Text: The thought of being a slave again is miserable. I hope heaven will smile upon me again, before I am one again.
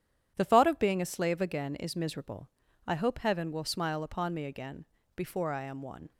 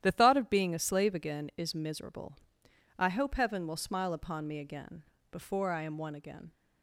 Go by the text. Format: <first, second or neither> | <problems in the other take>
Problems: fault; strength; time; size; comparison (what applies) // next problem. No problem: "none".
second | starts louder than the rest; strong; until 1.3 s; 10 dB; strong in the second // stops before "again"; at 6.1 s